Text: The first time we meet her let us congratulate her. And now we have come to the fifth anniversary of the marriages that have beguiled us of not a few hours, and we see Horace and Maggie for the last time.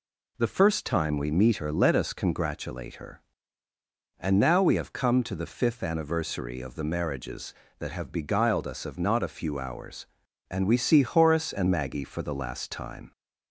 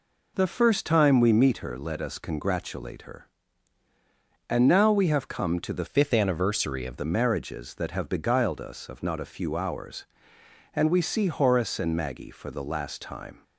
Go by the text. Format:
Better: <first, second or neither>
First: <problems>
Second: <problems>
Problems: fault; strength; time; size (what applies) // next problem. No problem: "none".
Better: first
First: none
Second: changes voice from "fifth" to "of"; from 5.8 to 6.9 s; 1.1 s long